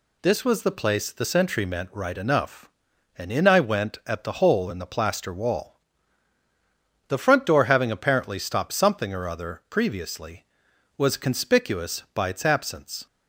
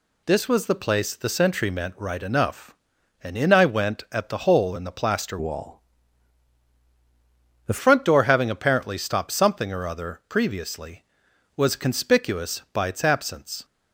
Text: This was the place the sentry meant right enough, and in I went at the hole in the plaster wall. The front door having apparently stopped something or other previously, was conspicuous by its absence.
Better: first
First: none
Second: changes voice from "wall" to "The"; from 5.3 to 7.7 s; 2.4 s long

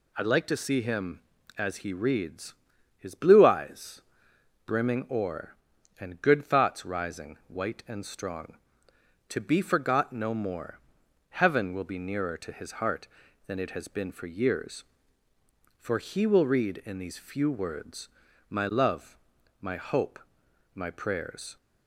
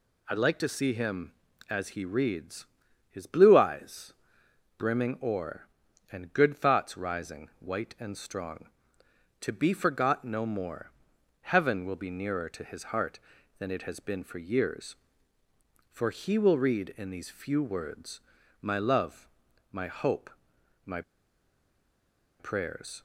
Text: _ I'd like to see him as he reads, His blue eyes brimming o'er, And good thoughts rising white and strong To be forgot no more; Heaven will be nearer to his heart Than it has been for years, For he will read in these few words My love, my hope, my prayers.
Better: first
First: pauses between "eyes" and "brimming"; noticeable; at 4.0 s; 0.64 s long // pauses between "words" and "My"; at 18.0 s; 0.40 s long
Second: pauses between "eyes" and "brimming"; noticeable; at 4.1 s; 0.64 s long // pauses between "words" and "My"; at 18.2 s; 0.40 s long // pauses between "my" and "prayers"; strong; at 21.0 s; 1.3 s long

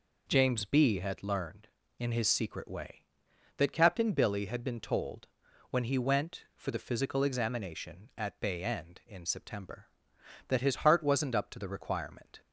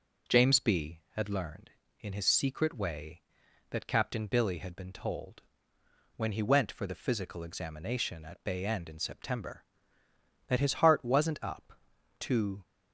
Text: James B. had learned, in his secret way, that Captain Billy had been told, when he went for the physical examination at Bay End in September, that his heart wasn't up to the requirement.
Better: first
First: none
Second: stops before "the requirement"; at 12.6 s

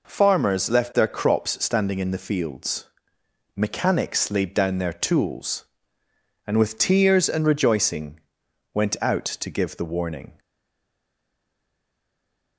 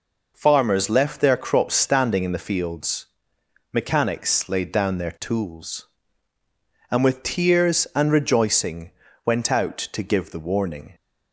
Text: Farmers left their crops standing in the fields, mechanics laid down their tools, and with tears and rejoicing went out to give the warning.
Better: second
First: pauses between "rejoicing" and "went"; noticeable; at 8.1 s; 0.54 s long // stays silent after the last word; from 10.3 s on; 2.2 s long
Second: pauses between "rejoicing" and "went"; slight; at 8.9 s; 0.34 s long

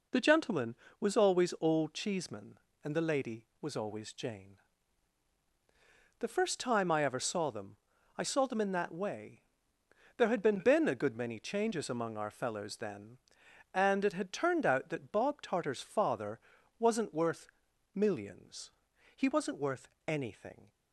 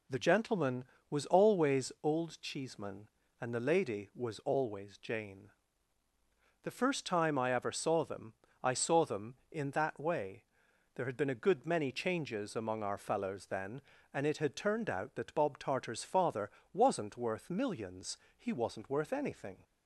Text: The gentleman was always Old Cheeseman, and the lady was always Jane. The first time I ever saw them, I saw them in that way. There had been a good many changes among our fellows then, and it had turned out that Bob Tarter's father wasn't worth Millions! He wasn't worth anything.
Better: second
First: says "been" twice; at 10.5 s // pauses between "father" and "wasn't"; at 16.3 s; 0.40 s long // pauses between "worth" and "Millions"; noticeable; at 17.4 s; 0.46 s long // pauses between "worth" and "anything"; slight; at 19.8 s; 0.18 s long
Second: pauses between "father" and "wasn't"; slight; at 16.4 s; 0.24 s long

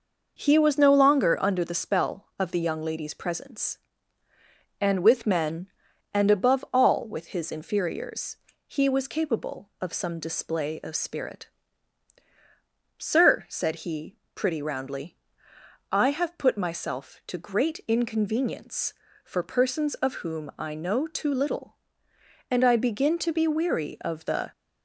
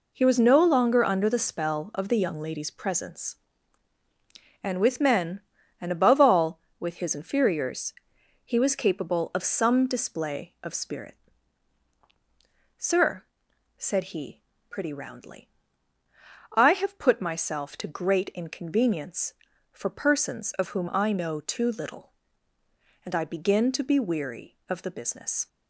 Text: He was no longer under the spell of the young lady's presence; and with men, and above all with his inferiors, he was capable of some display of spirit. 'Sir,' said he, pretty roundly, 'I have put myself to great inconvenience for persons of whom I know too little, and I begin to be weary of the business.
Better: second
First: starts louder than the rest; noticeable; until 1.4 s; 6 dB // stops before "business"; at 24.5 s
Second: none

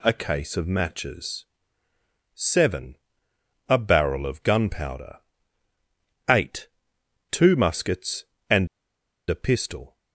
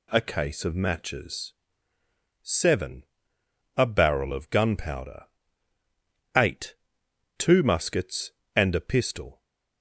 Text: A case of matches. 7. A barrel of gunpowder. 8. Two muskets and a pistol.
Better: second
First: pauses between "and" and "a"; noticeable; at 8.6 s; 0.63 s long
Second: none

